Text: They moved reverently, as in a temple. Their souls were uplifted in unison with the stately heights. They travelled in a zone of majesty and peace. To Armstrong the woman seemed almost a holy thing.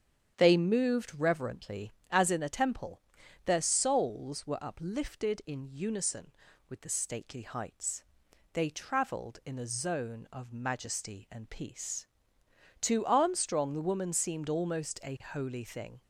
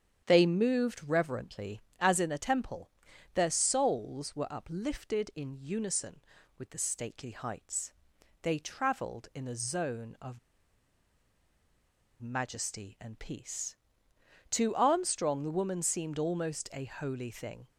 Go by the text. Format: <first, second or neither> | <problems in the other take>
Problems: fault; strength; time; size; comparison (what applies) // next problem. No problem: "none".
first | starts louder than the rest; strong; until 1.2 s; 8.5 dB; strong in the first // pauses between "of" and "majesty"; strong; at 10.3 s; 1.8 s long